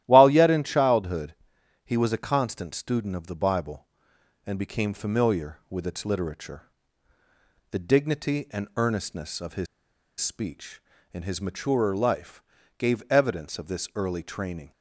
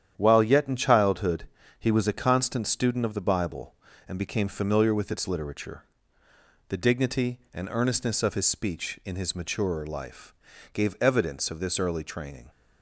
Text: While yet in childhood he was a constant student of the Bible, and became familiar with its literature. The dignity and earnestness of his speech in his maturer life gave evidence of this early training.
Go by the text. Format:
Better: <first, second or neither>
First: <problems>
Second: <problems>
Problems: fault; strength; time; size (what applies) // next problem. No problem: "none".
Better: second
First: starts louder than the rest; strong; until 1.0 s; 13.5 dB // pauses between "childhood" and "he"; noticeable; at 1.3 s; 0.52 s long // pauses between "his" and "speech"; noticeable; at 9.6 s; 0.54 s long // pauses between "life" and "gave"; at 12.4 s; 0.38 s long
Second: starts louder than the rest; strong; until 1.1 s; 9.5 dB // pauses between "childhood" and "he"; slight; at 1.4 s; 0.32 s long // pauses between "life" and "gave"; at 10.3 s; 0.38 s long